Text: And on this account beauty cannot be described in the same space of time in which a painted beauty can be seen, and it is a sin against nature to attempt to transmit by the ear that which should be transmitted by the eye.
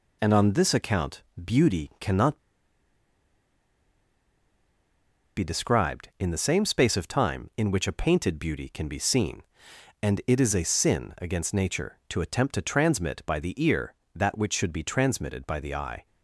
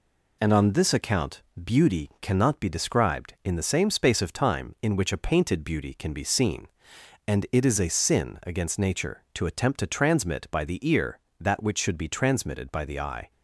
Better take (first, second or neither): second